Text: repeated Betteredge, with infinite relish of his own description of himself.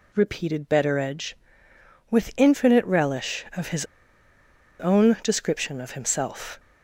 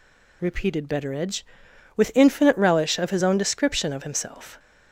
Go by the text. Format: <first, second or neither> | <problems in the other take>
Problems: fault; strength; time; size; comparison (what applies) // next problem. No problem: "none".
second | pauses between "his" and "own"; noticeable; at 3.8 s; 0.93 s long